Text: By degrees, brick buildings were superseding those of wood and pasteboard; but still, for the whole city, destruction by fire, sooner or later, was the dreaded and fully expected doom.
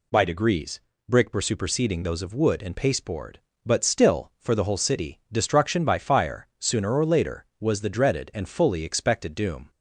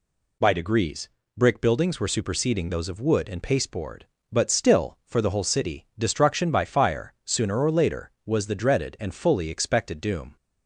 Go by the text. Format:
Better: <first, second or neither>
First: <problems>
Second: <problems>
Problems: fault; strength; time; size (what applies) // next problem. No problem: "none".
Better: second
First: skips "buildings"; at 1.3 s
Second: none